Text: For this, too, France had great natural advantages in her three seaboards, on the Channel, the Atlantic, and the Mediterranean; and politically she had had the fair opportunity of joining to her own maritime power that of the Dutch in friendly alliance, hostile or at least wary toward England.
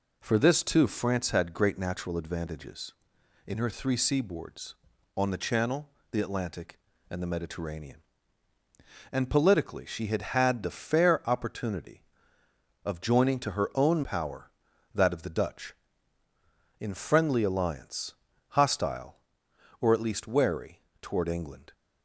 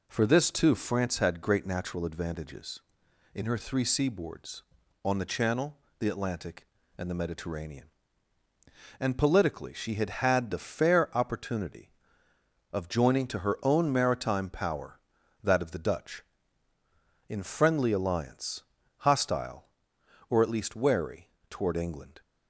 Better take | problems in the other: second | skips "maritime"; at 14.0 s // pauses between "wary" and "toward"; slight; at 20.8 s; 0.20 s long; slight in the second

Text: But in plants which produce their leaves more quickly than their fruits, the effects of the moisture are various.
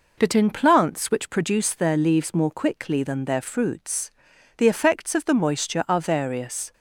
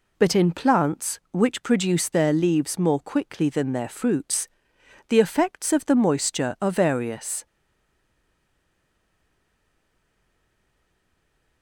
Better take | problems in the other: first | stays silent after the last word; strong; from 7.4 s on; 4.2 s long

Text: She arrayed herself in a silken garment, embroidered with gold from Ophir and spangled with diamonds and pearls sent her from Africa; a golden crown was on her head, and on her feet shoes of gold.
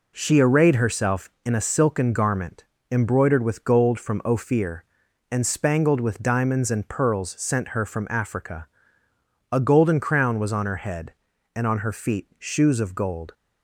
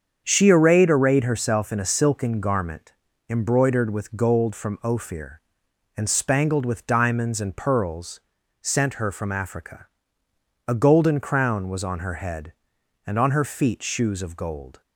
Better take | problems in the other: first | starts louder than the rest; strong; until 1.2 s; 7 dB // says "arrayed" twice; at 0.8 s // pauses between "pearls" and "sent"; at 8.1 s; 0.42 s long

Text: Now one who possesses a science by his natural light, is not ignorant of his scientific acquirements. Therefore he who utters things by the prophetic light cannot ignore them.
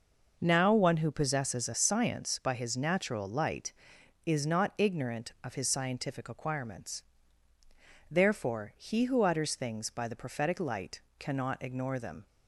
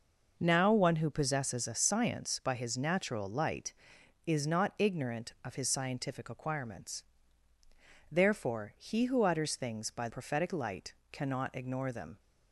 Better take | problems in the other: first | skips "the"; at 10.0 s // pauses between "light" and "cannot"; slight; at 10.9 s; 0.18 s long; slight in the first

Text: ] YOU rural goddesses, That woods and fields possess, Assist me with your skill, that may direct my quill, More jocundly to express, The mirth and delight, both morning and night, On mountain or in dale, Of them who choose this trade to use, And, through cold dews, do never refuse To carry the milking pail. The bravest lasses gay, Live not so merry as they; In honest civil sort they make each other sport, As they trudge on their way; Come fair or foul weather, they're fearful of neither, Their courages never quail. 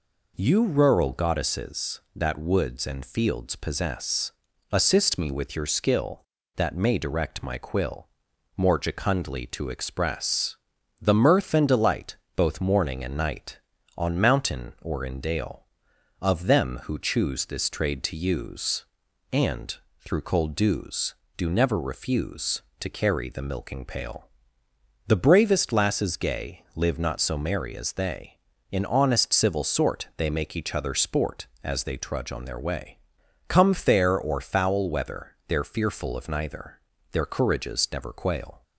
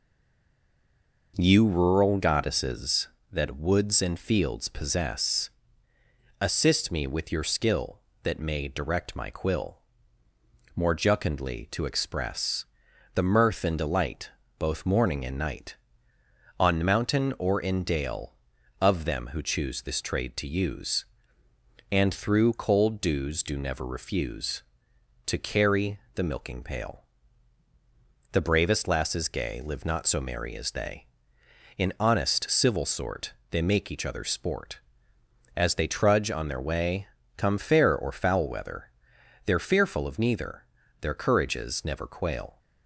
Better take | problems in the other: first | stays silent before the first word; noticeable; until 1.3 s; 1.3 s long // pauses between "carry" and "the"; slight; at 25.9 s; 0.16 s long // pauses between "sort" and "they"; slight; at 33.3 s; 0.18 s long

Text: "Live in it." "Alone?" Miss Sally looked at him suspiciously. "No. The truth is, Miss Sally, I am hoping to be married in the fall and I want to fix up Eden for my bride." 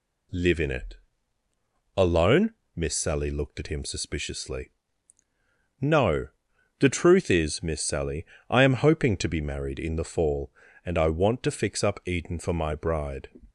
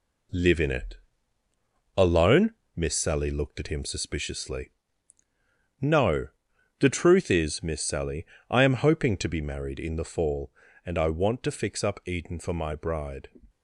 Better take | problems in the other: first | gets quieter; noticeable; throughout; 5 dB

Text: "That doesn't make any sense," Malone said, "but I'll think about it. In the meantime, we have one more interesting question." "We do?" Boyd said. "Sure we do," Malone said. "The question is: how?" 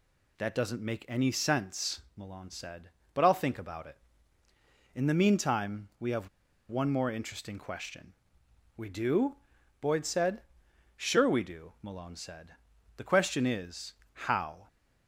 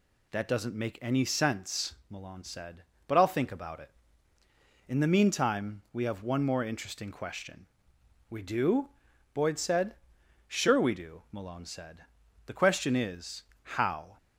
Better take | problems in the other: second | pauses between "have" and "one"; at 6.2 s; 0.40 s long

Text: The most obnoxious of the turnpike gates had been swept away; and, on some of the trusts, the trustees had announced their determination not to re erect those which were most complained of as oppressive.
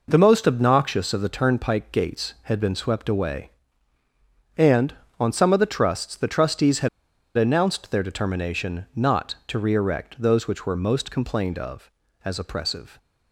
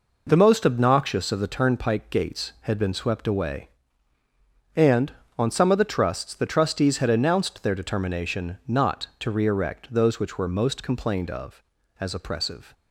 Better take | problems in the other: second | pauses between "had" and "announced"; noticeable; at 6.8 s; 0.47 s long

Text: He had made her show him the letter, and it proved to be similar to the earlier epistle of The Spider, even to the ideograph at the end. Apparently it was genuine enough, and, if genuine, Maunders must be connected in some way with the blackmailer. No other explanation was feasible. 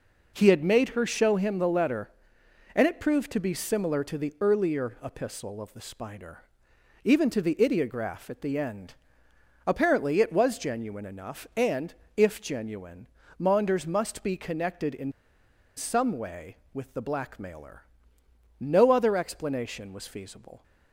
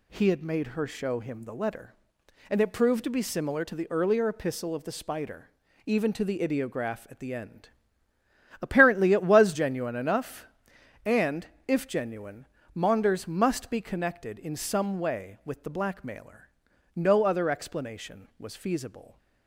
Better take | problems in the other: second | pauses between "in" and "some"; noticeable; at 15.1 s; 0.64 s long

